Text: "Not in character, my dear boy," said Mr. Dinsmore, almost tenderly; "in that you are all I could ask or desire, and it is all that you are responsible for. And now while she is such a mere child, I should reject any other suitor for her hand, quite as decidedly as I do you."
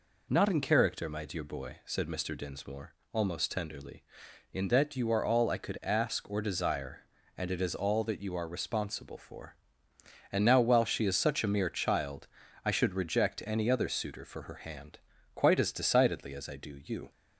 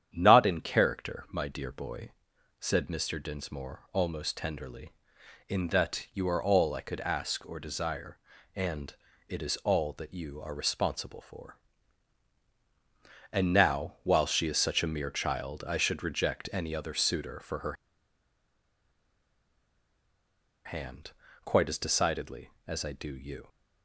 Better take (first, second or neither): first